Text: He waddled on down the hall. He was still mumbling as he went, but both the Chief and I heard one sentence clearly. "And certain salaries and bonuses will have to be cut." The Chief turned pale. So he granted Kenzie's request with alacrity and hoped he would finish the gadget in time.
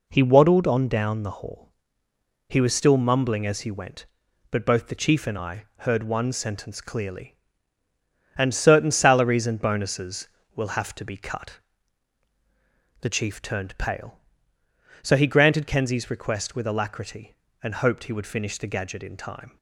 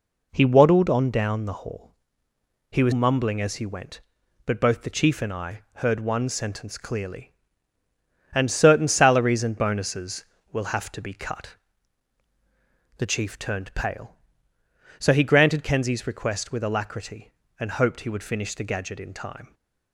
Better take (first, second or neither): first